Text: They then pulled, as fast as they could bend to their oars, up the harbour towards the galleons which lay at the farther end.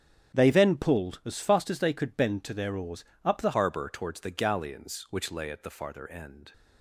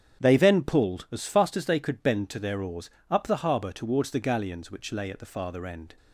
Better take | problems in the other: second | starts louder than the rest; strong; until 1.3 s; 9 dB; strong in the second // changes voice at "harbour"; from 3.5 s on; 3.0 s long

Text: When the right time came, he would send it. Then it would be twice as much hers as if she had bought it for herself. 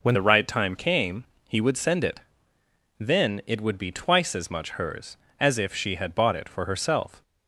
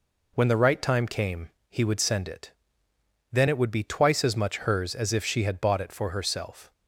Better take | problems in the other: second | changes voice at "the"; from 0.1 s on; 7.1 s long

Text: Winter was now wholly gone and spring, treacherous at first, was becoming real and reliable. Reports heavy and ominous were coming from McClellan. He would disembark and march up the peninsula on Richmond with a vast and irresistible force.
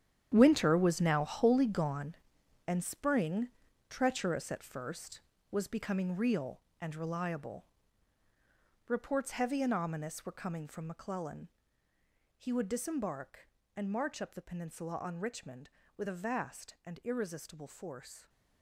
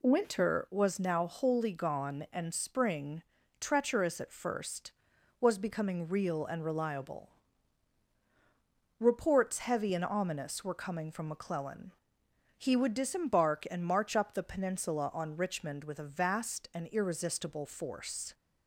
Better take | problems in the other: second | gets quieter; strong; throughout; 13 dB

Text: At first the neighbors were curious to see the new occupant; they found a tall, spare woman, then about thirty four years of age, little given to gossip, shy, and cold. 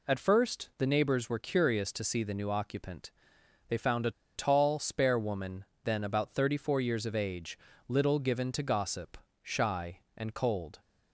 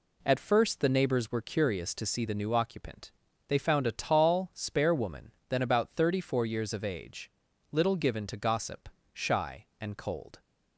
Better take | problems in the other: second | pauses between "a" and "tall"; slight; at 4.1 s; 0.24 s long

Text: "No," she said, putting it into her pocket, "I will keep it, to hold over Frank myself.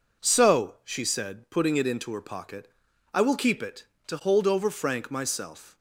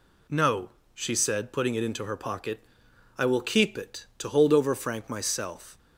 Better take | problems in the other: second | says "So" for "No"; at 0.2 s

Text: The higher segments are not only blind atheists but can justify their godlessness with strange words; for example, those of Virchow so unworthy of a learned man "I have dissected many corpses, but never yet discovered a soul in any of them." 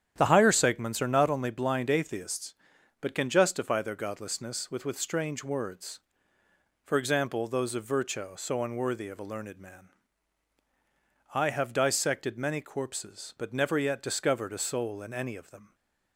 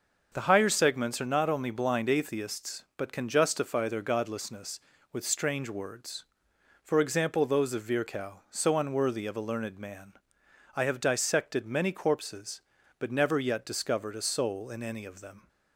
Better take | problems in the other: second | starts louder than the rest; strong; until 1.1 s; 9 dB; noticeable in the second // says "with" twice; at 4.8 s // pauses between "man" and "I"; strong; at 9.9 s; 1.4 s long; noticeable in the second

